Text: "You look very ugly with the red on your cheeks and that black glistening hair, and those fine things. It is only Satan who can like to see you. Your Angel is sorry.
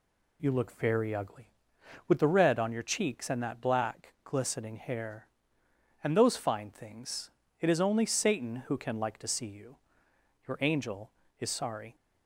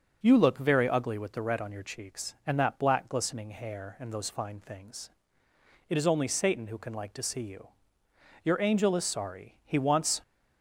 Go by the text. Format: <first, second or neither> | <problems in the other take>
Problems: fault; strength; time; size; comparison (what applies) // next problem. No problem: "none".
first | goes on to say "He wants"; from 9.6 s on; 0.56 s long